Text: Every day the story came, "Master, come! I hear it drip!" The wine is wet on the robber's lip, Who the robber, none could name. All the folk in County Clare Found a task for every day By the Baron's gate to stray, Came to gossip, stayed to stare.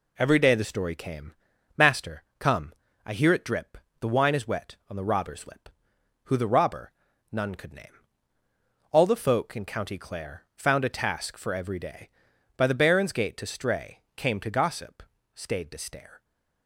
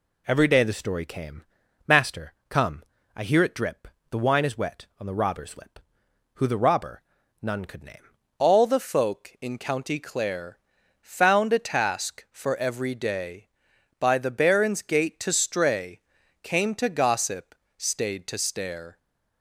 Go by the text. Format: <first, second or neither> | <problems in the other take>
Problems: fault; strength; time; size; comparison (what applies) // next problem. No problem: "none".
first | changes voice at "All"; from 8.3 s on; 10.6 s long // pauses between "Clare" and "Found"; at 10.5 s; 0.42 s long